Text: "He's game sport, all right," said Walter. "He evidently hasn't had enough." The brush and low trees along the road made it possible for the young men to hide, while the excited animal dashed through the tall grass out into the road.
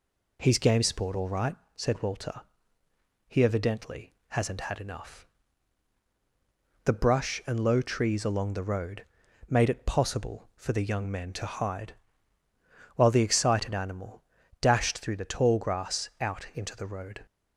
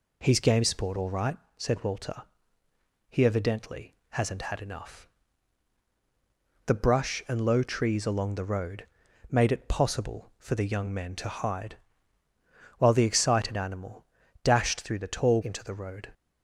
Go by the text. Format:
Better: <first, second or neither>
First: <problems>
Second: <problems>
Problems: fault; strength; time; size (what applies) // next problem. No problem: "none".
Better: first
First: pauses between "road" and "made"; noticeable; at 9.0 s; 0.46 s long // pauses between "animal" and "dashed"; at 14.2 s; 0.38 s long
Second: pauses between "road" and "made"; noticeable; at 8.8 s; 0.46 s long // pauses between "animal" and "dashed"; at 14.0 s; 0.38 s long // skips "grass out"; at 15.4 s